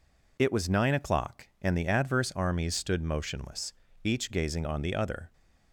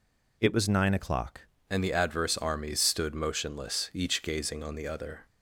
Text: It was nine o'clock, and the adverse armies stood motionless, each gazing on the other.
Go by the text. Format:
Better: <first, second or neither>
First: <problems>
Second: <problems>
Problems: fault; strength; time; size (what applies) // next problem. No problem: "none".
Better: first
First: none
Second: changes voice at "and"; from 1.6 s on; 3.6 s long